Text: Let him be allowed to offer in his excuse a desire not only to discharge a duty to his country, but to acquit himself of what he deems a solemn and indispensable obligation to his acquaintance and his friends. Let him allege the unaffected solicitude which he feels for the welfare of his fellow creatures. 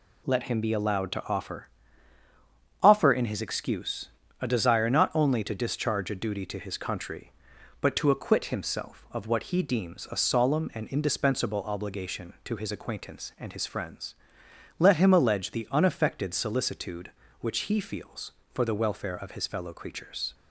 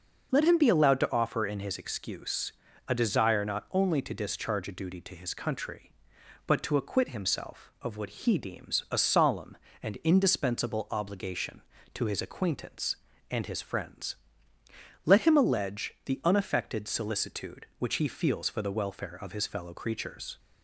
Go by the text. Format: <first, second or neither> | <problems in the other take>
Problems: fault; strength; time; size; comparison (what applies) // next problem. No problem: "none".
second | says "offer" twice; at 2.8 s // pauses between "excuse" and "a"; slight; at 4.0 s; 0.32 s long; slight in the second